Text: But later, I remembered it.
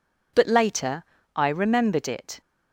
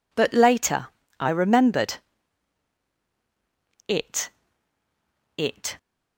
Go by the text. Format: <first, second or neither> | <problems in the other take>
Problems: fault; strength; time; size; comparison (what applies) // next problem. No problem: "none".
first | pauses between "remembered" and "it"; strong; at 1.9 s; 1.9 s long // says "it" twice; at 5.3 s